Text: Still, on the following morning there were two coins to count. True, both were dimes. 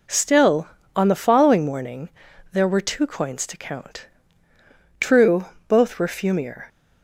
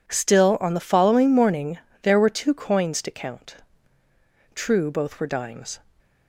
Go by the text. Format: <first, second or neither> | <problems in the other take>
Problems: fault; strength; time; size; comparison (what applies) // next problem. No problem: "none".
second | pauses between "morning" and "there"; at 2.1 s; 0.42 s long; slight in the second // says "fumier" for "dimes"; at 6.0 s